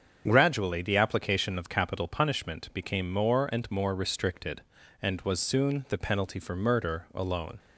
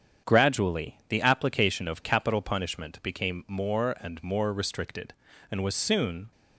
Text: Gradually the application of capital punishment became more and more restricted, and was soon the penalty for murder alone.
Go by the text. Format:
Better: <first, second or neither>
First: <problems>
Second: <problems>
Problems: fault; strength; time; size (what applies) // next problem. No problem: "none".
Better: first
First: starts louder than the rest; strong; until 1.2 s; 7.5 dB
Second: starts louder than the rest; strong; until 1.3 s; 8 dB // stops before "the penalty for murder alone"; at 6.3 s